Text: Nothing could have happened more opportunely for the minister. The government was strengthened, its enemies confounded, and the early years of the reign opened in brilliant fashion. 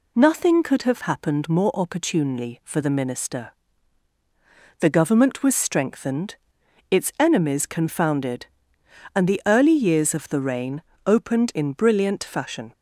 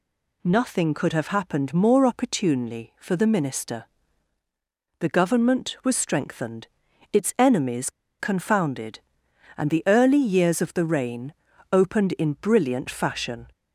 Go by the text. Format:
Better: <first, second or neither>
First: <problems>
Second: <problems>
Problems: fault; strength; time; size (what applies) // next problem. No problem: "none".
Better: first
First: pauses between "reign" and "opened"; slight; at 10.7 s; 0.26 s long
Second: pauses between "enemies" and "confounded"; slight; at 7.8 s; 0.29 s long // pauses between "reign" and "opened"; at 11.3 s; 0.40 s long